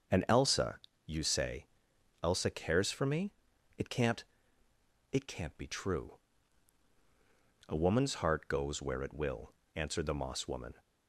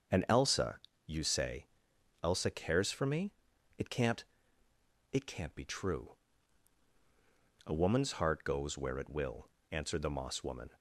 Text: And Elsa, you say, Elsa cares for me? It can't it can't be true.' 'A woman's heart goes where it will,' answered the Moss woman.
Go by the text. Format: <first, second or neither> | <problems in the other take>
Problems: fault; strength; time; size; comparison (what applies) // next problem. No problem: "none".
neither | starts louder than the rest; the same in both // pauses between "can't" and "it"; noticeable; the same in both